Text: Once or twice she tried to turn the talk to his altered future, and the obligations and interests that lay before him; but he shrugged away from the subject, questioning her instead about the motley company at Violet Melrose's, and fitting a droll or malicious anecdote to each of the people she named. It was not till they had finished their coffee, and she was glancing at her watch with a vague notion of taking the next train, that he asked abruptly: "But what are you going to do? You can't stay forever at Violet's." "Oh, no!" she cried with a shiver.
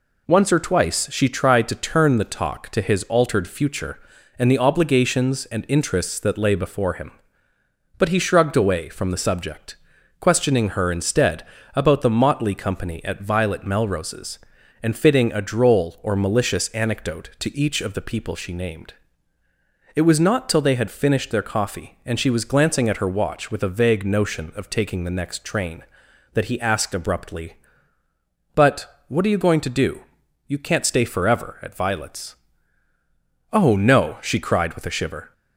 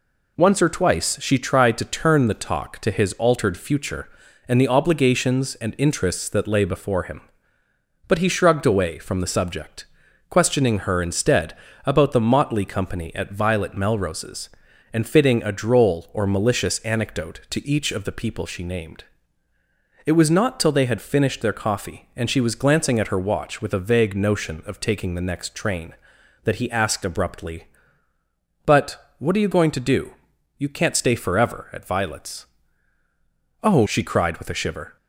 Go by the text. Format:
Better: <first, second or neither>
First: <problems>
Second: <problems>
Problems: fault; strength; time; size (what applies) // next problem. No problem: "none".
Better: first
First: pauses between "instead" and "about"; slight; at 11.4 s; 0.30 s long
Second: pauses between "instead" and "about"; slight; at 11.5 s; 0.30 s long // skips "no"; at 33.8 s